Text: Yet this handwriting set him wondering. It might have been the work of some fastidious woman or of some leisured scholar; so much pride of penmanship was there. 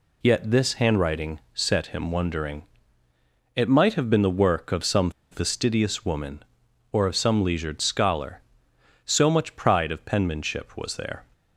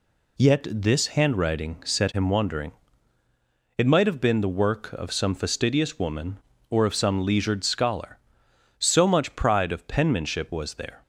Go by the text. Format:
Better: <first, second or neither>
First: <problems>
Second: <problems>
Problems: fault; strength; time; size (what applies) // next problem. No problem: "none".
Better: second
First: pauses between "some" and "fastidious"; slight; at 5.0 s; 0.21 s long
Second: none